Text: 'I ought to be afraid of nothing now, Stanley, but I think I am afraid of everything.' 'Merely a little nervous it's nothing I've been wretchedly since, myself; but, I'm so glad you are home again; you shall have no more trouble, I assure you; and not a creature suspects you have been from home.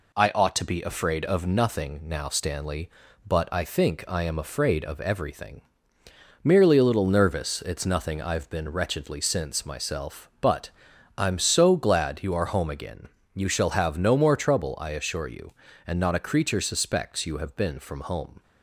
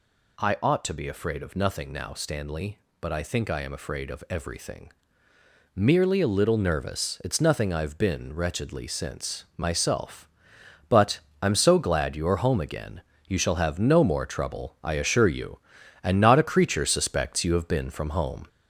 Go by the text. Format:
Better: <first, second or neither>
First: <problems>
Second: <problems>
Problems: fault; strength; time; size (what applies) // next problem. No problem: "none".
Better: first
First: none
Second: gets louder; noticeable; throughout; 4 dB